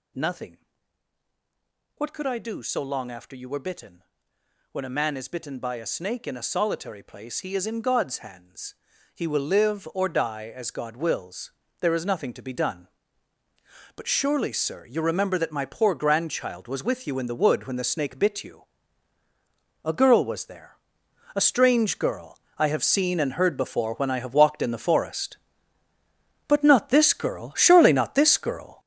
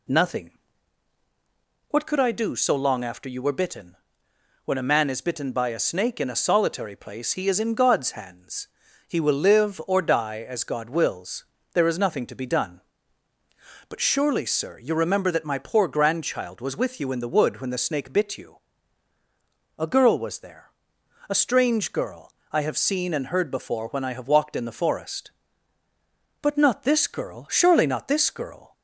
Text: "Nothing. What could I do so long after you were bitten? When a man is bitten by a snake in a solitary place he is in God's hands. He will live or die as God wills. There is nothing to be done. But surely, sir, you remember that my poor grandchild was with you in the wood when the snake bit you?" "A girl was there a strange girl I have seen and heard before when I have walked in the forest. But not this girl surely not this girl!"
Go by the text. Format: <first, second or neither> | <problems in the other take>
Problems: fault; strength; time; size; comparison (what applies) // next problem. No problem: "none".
second | gets louder; strong; throughout; 8.5 dB // pauses between "there" and "a"; noticeable; at 20.7 s; 0.58 s long; noticeable in the second // pauses between "girl" and "I"; slight; at 22.3 s; 0.18 s long; slight in the second